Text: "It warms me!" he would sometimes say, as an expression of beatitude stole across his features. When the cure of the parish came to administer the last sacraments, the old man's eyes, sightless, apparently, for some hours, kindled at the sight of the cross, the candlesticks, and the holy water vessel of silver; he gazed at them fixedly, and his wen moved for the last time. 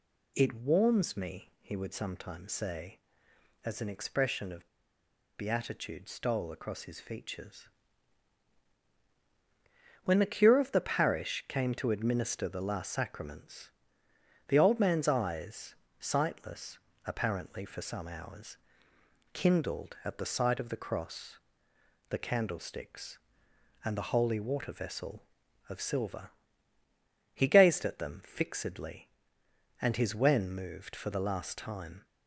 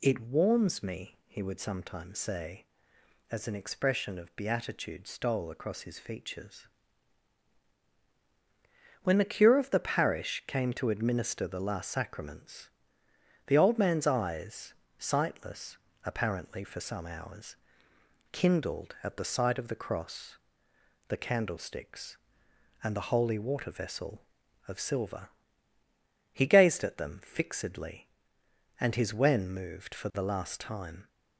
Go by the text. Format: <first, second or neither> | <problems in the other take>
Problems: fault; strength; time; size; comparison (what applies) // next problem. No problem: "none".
second | pauses between "of" and "beatitude"; noticeable; at 4.6 s; 0.67 s long